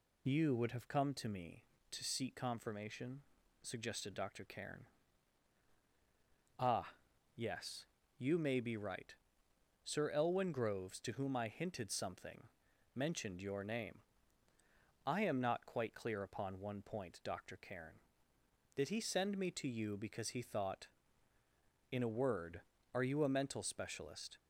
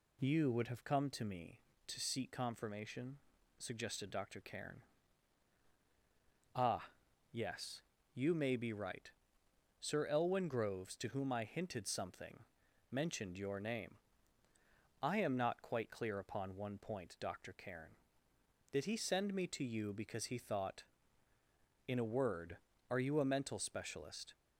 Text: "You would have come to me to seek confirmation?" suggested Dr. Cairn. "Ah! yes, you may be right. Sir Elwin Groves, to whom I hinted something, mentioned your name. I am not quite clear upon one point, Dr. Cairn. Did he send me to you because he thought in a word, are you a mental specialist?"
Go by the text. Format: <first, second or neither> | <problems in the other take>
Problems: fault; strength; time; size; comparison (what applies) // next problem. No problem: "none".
second | loses the start of "You"; at 0.2 s; 25 ms